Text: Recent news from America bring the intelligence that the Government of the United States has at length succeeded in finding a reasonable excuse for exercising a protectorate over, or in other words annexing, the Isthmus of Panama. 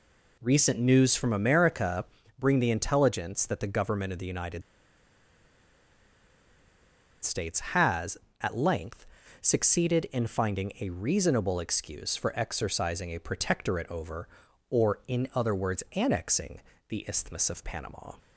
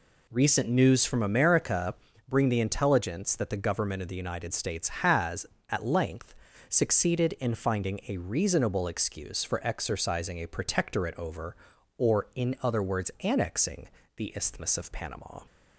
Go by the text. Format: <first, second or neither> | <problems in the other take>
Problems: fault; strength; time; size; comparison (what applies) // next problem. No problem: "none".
second | pauses between "America" and "bring"; slight; at 2.0 s; 0.34 s long; slight in the second // pauses between "United" and "States"; strong; at 4.6 s; 2.6 s long // pauses between "length" and "succeeded"; slight; at 9.0 s; 0.34 s long; slight in the second